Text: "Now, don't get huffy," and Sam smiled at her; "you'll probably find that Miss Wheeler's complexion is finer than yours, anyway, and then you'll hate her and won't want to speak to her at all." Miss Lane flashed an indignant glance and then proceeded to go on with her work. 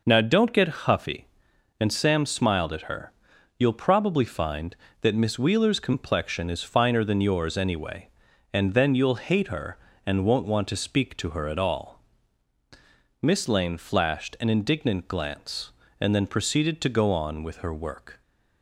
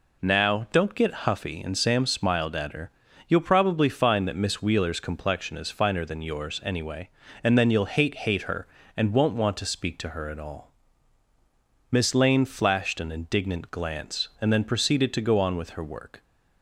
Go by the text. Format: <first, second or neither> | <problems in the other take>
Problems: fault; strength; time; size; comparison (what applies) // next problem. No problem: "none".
first | says "hate" twice; at 8.1 s